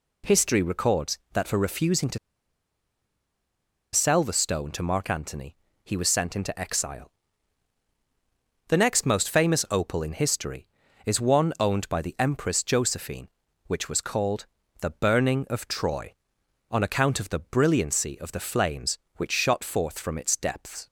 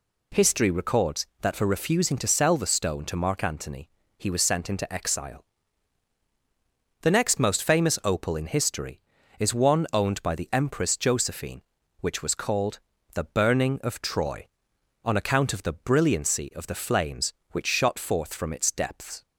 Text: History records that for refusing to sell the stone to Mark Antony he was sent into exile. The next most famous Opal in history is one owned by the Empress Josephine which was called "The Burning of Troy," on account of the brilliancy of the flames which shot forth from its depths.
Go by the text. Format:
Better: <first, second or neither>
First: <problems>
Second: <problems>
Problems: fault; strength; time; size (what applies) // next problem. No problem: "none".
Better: second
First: pauses between "to" and "sell"; strong; at 2.1 s; 1.7 s long // pauses between "Antony" and "he"; slight; at 5.5 s; 0.30 s long // pauses between "called" and "The"; slight; at 14.4 s; 0.34 s long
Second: pauses between "Antony" and "he"; slight; at 3.8 s; 0.30 s long // pauses between "called" and "The"; slight; at 12.7 s; 0.34 s long